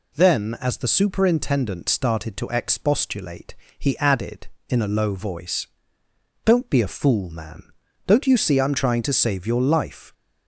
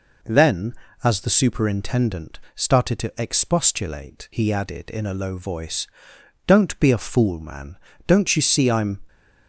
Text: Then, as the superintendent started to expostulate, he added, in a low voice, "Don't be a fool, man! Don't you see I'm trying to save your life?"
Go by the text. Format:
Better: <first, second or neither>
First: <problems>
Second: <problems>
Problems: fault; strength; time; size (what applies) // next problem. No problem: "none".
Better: first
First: none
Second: pauses between "superintendent" and "started"; slight; at 2.3 s; 0.16 s long // stops before "trying to save your life"; at 9.0 s